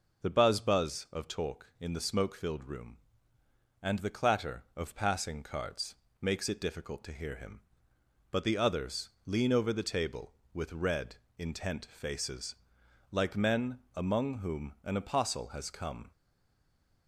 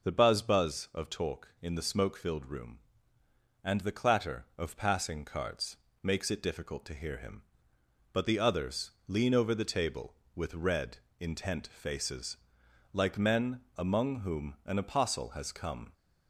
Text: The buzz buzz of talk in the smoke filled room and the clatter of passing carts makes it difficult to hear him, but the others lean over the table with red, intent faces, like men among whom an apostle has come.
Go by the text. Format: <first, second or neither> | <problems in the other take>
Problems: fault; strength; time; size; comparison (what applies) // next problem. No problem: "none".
second | pauses between "carts" and "makes"; slight; at 5.9 s; 0.26 s long; slight in the second // pauses between "others" and "lean"; slight; at 9.0 s; 0.16 s long; slight in the second // pauses between "men" and "among"; slight; at 13.7 s; 0.16 s long; slight in the second // stays silent after the last word; slight; from 16.1 s on; 0.9 s long